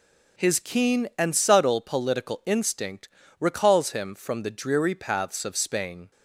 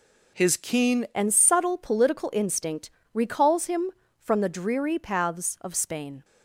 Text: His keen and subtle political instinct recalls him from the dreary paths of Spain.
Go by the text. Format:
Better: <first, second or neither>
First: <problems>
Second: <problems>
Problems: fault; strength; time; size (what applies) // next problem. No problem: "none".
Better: first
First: pauses between "instinct" and "recalls"; slight; at 3.0 s; 0.32 s long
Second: changes voice at "and"; from 1.1 s on; 5.1 s long // pauses between "instinct" and "recalls"; slight; at 2.9 s; 0.24 s long